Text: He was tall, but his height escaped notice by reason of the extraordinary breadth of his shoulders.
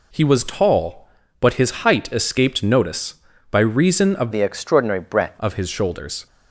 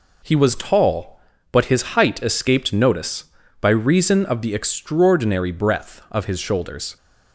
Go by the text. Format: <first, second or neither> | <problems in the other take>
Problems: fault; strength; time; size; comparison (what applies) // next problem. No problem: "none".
second | changes voice from "the" to "breadth"; from 4.3 to 5.3 s; 1.0 s long